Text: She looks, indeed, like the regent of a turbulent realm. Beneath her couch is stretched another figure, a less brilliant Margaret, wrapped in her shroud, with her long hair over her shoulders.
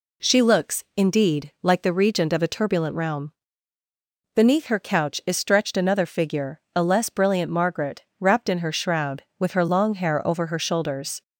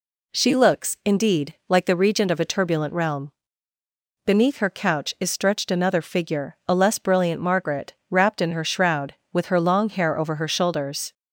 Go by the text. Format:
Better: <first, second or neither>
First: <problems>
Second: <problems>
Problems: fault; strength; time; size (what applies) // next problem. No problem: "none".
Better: neither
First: none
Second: none